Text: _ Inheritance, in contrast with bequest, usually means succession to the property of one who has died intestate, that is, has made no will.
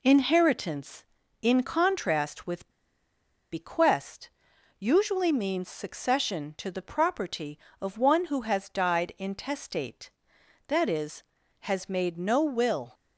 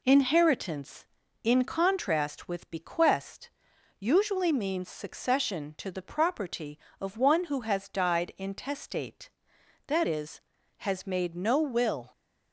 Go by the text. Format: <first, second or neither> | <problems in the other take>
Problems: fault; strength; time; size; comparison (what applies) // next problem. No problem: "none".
second | pauses between "with" and "bequest"; noticeable; at 2.6 s; 0.85 s long